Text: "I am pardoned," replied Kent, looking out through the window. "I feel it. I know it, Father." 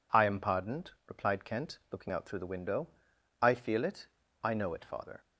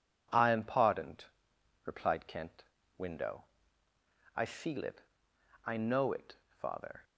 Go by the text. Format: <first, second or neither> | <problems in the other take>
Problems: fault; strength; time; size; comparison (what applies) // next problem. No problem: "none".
first | skips "looking out through the"; at 2.8 s